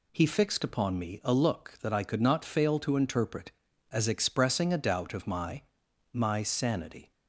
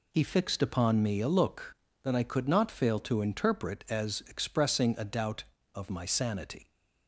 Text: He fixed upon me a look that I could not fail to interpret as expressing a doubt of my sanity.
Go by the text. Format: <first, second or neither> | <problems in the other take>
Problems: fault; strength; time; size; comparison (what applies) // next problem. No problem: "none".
second | says "my" twice; at 6.1 s